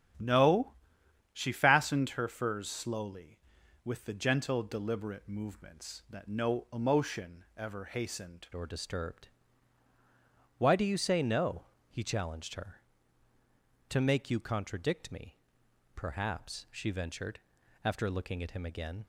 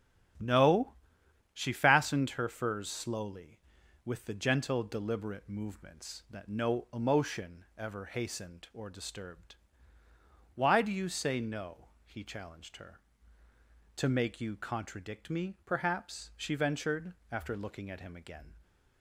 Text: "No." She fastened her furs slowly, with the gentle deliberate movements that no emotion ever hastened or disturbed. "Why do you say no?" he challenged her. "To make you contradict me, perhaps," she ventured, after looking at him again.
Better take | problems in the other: second | starts louder than the rest; strong; until 1.7 s; 9.5 dB; strong in the second // changes voice at "or"; from 8.5 s on; 10.5 s long

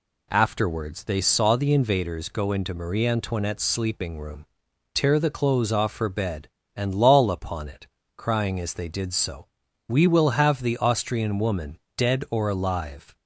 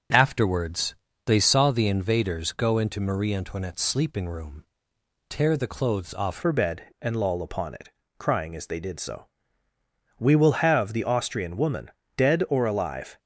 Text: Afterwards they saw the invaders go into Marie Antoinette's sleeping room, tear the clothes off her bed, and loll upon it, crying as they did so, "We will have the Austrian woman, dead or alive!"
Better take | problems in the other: first | starts louder than the rest; until 1.4 s; 7 dB // pauses between "Afterwards" and "they"; slight; at 0.9 s; 0.32 s long // changes voice at "her"; from 6.3 s on; 6.8 s long

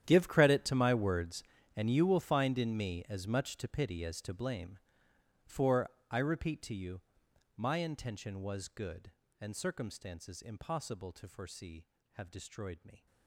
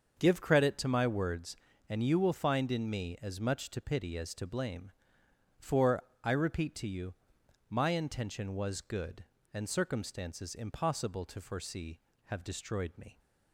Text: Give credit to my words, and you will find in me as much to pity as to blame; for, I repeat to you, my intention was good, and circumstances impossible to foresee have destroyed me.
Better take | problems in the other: second | gets quieter; strong; throughout; 18.5 dB // starts louder than the rest; strong; until 1.0 s; 10.5 dB; also in the second

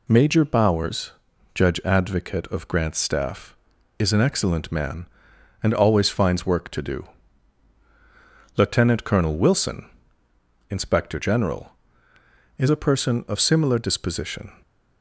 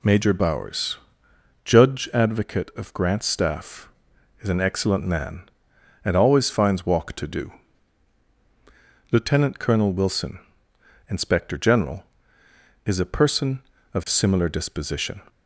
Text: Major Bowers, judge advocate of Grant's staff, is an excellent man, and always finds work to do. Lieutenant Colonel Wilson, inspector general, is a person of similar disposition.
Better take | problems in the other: first | says "walk" for "work"; at 6.8 s

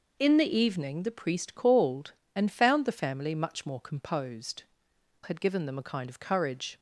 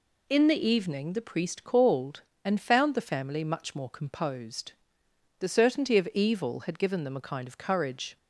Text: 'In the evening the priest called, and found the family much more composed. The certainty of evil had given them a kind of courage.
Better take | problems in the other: second | skips "The certainty of evil"; at 4.9 s

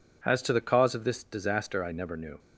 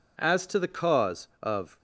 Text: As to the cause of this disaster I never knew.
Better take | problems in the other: first | stops before "this disaster I never knew"; at 1.7 s

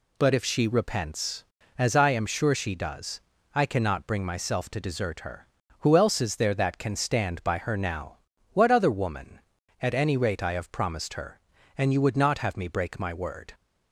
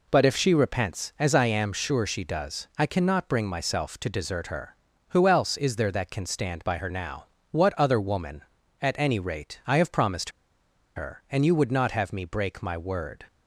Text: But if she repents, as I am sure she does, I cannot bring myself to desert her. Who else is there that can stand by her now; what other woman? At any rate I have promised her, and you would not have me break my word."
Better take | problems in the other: first | pauses between "promised" and "her"; noticeable; at 10.2 s; 0.66 s long

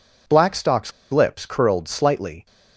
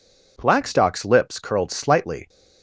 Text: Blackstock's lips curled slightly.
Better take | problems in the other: second | pauses between "Blackstock's" and "lips"; slight; at 0.9 s; 0.20 s long

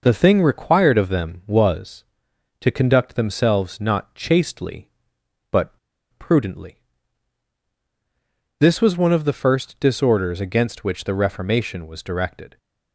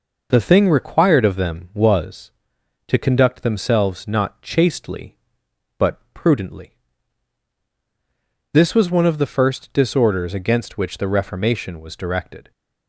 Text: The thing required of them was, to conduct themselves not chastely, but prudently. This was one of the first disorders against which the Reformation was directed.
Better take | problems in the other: second | pauses between "but" and "prudently"; at 5.7 s; 0.45 s long

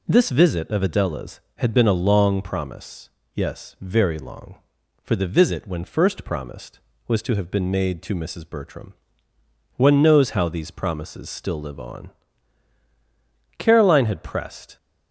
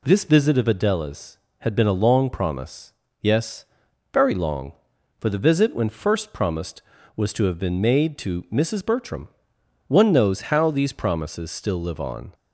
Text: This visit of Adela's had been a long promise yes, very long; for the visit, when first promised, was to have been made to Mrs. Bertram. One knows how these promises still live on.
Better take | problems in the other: second | pauses between "promise" and "yes"; slight; at 3.0 s; 0.26 s long; slight in the second // goes on to say "Caroline had pressed"; noticeable; from 13.5 s on; 1.1 s long

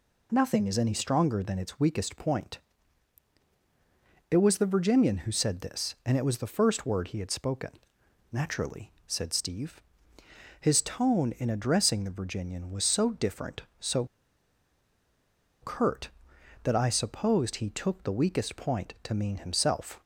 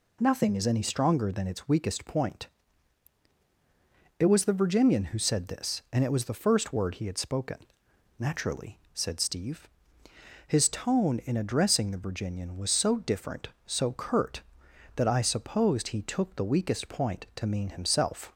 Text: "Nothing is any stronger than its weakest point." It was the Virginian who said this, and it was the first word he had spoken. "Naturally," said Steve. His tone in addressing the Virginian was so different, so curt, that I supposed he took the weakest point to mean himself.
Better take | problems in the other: second | pauses between "so" and "curt"; strong; at 14.0 s; 1.5 s long

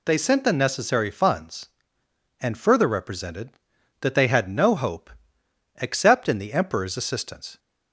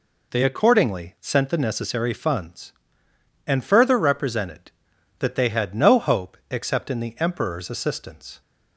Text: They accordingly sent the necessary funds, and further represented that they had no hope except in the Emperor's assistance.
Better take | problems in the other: second | skips "accordingly"; at 0.1 s // pauses between "hope" and "except"; noticeable; at 5.1 s; 0.70 s long

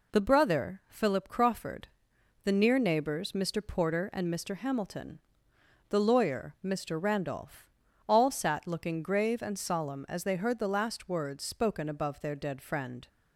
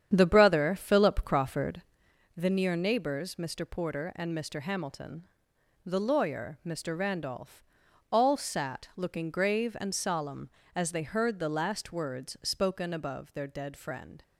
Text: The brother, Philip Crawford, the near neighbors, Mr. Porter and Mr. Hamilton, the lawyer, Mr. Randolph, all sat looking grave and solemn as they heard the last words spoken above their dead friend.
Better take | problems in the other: first | starts louder than the rest; strong; until 2.1 s; 9 dB

